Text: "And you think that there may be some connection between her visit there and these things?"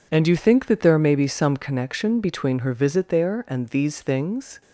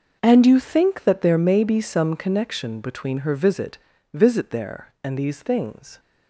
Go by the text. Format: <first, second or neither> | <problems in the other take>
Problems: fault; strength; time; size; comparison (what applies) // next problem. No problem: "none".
first | starts louder than the rest; until 1.2 s; 6 dB // says "visit" twice; at 4.1 s